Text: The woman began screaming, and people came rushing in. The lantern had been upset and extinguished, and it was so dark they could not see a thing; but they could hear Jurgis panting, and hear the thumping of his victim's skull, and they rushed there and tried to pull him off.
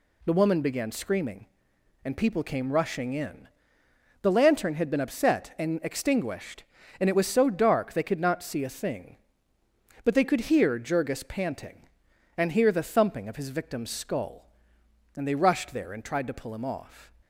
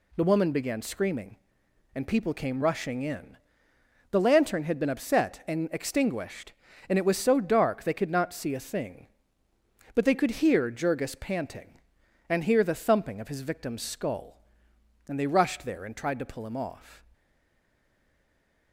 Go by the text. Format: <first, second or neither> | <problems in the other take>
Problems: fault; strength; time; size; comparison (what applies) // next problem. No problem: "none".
first | stays silent after the last word; noticeable; from 17.1 s on; 1.6 s long